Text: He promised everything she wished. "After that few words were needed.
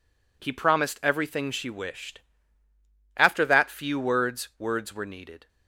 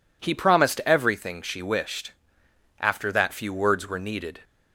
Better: second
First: says "words" twice; at 4.5 s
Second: none

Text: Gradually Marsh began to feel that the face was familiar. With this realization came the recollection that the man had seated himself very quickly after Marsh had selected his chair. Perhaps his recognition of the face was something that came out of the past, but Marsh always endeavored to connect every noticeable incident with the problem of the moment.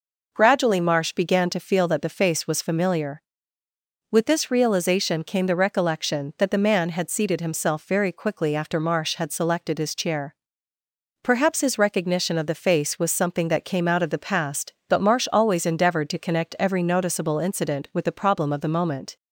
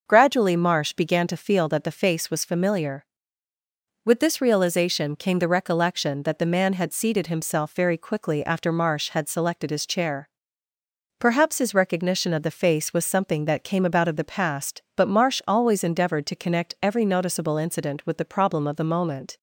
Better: first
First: none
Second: says "about" for "out"; at 13.8 s

